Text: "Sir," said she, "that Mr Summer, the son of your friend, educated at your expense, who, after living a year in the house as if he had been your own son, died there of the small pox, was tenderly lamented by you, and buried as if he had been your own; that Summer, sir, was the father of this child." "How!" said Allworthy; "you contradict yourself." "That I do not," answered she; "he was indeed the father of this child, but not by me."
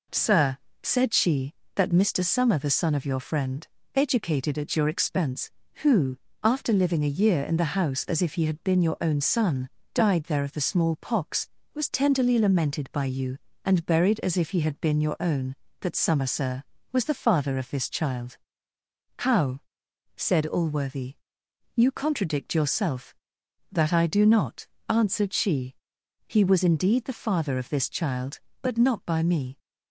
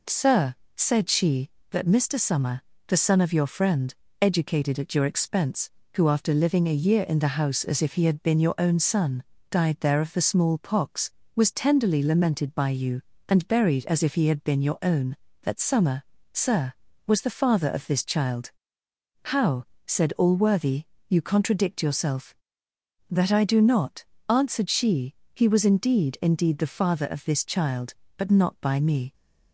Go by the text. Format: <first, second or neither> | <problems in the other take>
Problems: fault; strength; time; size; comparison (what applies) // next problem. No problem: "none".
first | says "indeed" twice; at 26.2 s